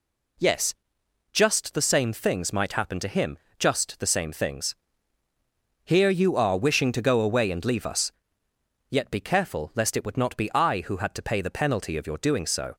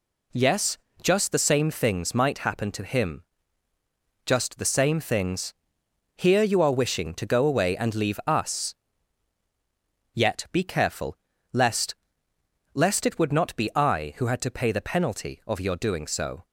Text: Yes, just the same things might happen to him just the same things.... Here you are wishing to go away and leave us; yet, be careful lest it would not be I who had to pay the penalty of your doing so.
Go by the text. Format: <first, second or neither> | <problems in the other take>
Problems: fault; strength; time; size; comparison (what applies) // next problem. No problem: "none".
first | pauses between "him" and "just"; at 3.2 s; 1.0 s long; slight in the first // pauses between "careful" and "lest"; at 11.1 s; 0.38 s long // says "lest" twice; at 12.7 s